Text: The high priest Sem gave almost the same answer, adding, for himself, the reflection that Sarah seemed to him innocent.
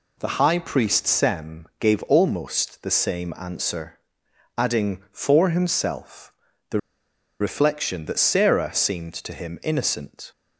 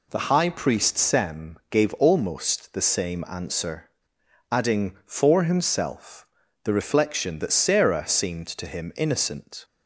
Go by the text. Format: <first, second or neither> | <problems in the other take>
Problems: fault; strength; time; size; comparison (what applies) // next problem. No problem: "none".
second | pauses between "the" and "reflection"; noticeable; at 6.7 s; 0.61 s long